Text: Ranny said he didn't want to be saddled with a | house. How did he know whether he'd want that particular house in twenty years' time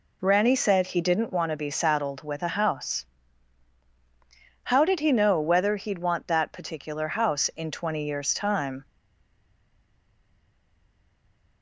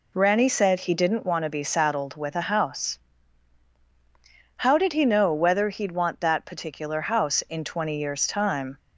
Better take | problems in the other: second | stays silent after the last word; strong; from 8.8 s on; 2.8 s long

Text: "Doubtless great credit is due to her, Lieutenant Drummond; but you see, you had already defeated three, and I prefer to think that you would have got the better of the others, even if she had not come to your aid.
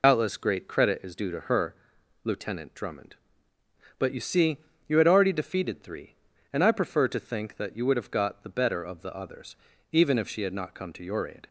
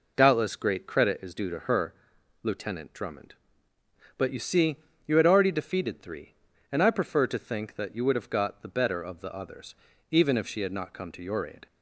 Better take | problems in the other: second | loses the start of "Doubtless"; at 0.0 s; 70 ms

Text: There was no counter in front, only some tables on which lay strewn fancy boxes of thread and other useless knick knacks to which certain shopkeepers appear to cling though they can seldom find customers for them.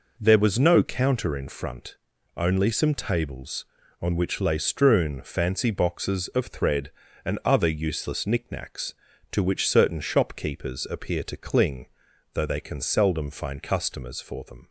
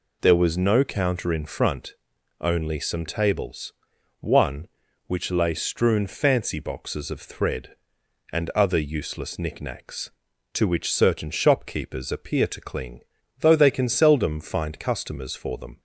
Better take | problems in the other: first | says "one" for "on"; at 4.1 s // pauses between "cling" and "though"; at 12.9 s; 0.40 s long; noticeable in the first

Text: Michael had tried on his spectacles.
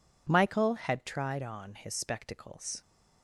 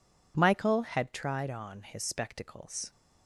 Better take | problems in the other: neither | none

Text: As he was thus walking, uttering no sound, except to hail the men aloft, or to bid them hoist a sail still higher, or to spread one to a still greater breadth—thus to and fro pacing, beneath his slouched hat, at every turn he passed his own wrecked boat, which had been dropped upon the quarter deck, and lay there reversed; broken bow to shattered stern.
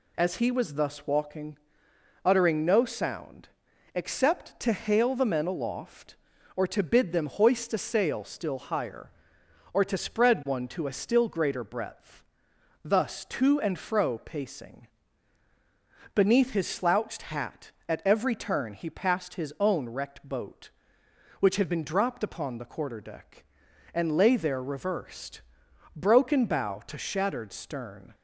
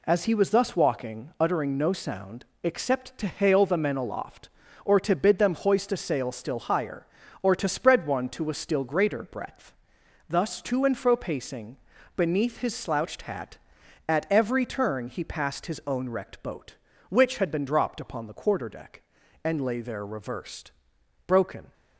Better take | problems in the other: first | stops before "bow to shattered stern"; at 21.7 s

